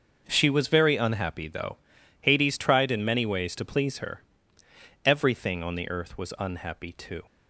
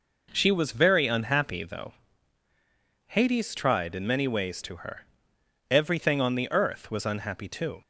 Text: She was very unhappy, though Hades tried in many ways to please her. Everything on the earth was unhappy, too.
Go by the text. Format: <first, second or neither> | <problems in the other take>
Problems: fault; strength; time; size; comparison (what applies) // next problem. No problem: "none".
first | pauses between "though" and "Hades"; at 1.9 s; 1.1 s long; also in the first // skips "please"; at 4.7 s